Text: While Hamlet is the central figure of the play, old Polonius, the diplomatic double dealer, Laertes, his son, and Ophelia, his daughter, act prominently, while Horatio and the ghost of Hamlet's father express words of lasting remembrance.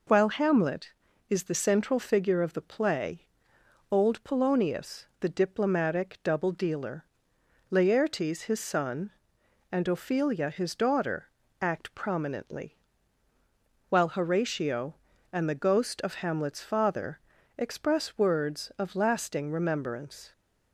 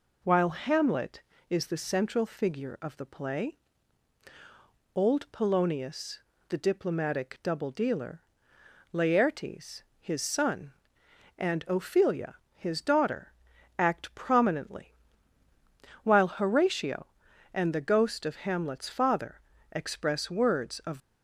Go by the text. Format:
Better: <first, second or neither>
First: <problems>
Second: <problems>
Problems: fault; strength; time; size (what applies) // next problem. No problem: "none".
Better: first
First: pauses between "father" and "express"; at 17.1 s; 0.40 s long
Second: pauses between "father" and "express"; slight; at 19.4 s; 0.32 s long // stops before "lasting remembrance"; at 21.0 s